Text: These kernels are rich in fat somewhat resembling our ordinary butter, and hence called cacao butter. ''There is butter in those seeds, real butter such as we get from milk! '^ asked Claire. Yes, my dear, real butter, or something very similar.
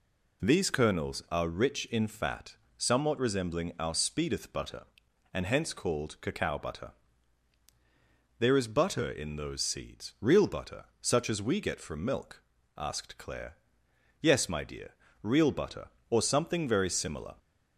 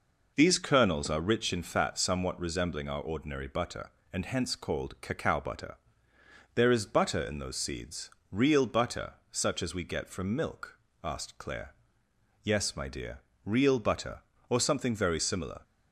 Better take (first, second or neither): second